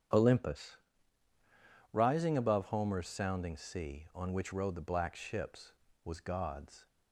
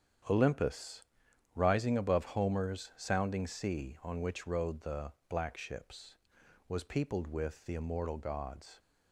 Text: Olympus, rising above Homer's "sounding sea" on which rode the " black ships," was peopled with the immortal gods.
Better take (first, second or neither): second